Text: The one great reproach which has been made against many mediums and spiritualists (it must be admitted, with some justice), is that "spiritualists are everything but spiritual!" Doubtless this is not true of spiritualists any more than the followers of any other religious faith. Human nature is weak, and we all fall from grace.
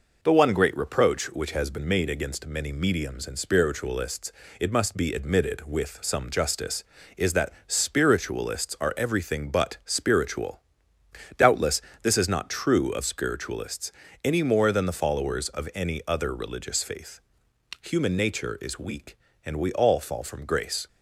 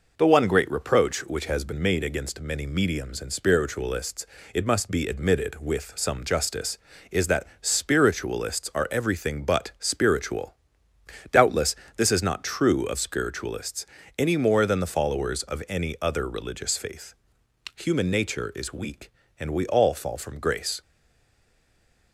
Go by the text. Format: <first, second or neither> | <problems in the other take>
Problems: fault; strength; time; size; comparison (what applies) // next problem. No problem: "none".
first | pauses between "Doubtless" and "this"; slight; at 11.7 s; 0.22 s long; slight in the first // pauses between "spiritualists" and "any"; slight; at 13.8 s; 0.28 s long; slight in the first // stays silent after the last word; noticeable; from 20.8 s on; 1.3 s long